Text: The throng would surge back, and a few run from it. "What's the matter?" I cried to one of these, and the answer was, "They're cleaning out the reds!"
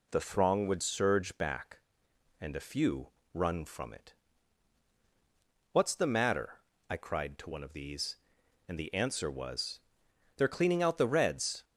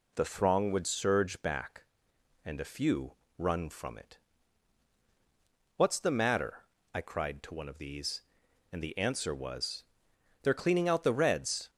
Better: neither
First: pauses between "few" and "run"; slight; at 3.1 s; 0.24 s long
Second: pauses between "few" and "run"; slight; at 3.1 s; 0.24 s long

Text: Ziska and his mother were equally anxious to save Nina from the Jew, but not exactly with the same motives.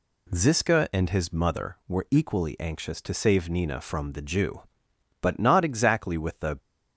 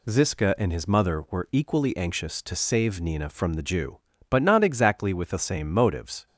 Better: second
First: stops before "same motives"; at 6.5 s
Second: none

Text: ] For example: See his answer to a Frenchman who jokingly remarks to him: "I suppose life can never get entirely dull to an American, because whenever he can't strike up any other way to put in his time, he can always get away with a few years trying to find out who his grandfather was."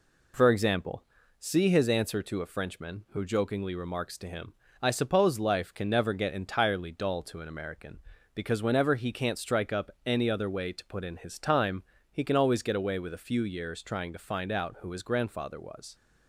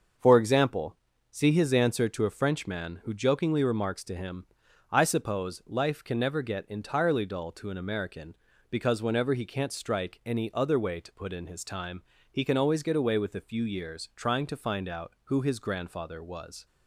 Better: first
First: none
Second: starts louder than the rest; until 1.5 s; 6.5 dB // skips "up"; at 10.2 s

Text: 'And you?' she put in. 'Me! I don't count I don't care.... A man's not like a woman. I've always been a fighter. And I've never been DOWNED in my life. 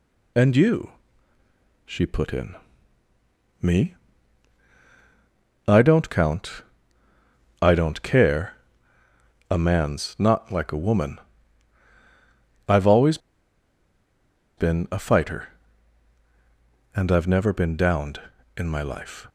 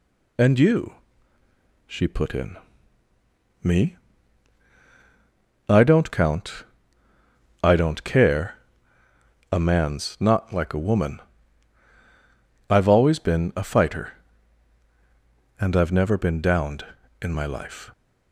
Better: second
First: pauses between "count" and "I"; at 6.6 s; 1.0 s long // pauses between "always" and "been"; strong; at 13.1 s; 1.3 s long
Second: pauses between "count" and "I"; at 6.6 s; 1.0 s long

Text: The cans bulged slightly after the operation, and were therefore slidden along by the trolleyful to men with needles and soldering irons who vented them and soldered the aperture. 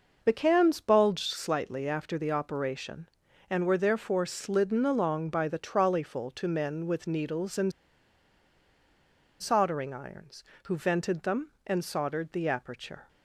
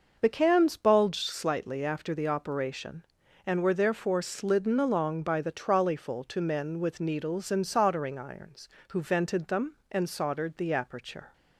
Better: second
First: pauses between "and" and "soldering"; strong; at 7.7 s; 1.6 s long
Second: none

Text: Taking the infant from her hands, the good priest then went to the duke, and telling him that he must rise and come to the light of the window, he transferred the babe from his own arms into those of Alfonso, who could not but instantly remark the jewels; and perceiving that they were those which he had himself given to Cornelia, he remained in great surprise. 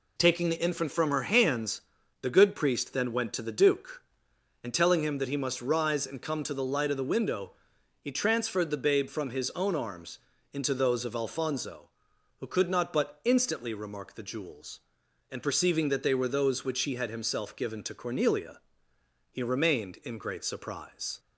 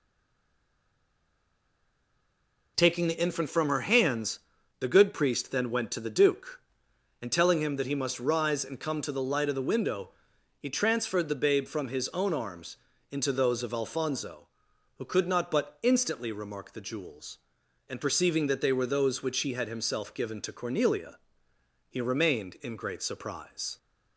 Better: first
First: pauses between "arms" and "into"; slight; at 10.1 s; 0.36 s long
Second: stays silent before the first word; strong; until 2.7 s; 2.7 s long // pauses between "arms" and "into"; slight; at 12.7 s; 0.36 s long

